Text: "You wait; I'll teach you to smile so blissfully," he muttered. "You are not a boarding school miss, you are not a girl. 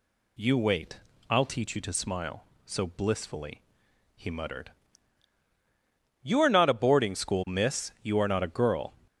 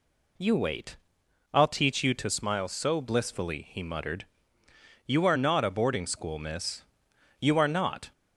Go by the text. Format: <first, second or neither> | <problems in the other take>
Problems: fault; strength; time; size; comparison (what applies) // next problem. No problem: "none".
first | stops before "a girl"; at 8.1 s